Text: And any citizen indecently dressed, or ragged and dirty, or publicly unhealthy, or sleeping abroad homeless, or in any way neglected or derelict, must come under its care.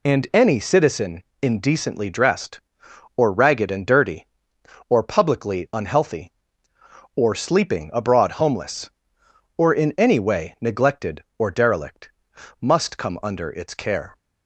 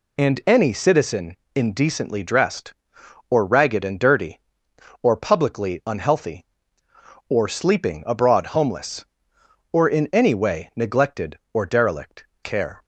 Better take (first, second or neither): first